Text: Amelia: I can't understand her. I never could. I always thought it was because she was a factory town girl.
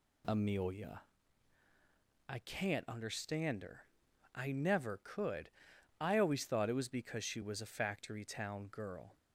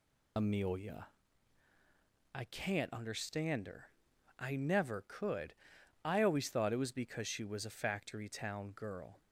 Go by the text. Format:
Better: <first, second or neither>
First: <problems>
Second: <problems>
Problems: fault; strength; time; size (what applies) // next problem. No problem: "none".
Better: first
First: none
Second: loses the start of "Amelia"; at 0.3 s; 55 ms